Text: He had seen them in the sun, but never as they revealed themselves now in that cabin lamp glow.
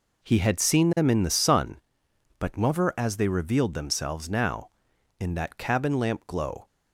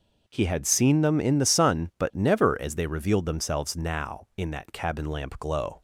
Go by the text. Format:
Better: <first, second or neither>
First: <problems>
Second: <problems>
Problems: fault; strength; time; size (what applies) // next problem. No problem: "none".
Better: neither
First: none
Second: none